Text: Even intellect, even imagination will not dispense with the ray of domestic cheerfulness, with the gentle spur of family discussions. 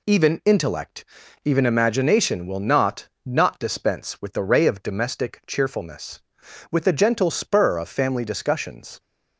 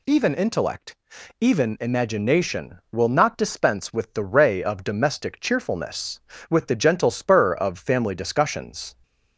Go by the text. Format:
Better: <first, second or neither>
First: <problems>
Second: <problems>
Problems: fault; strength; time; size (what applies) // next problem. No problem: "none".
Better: second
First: says "not" twice; at 3.2 s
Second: none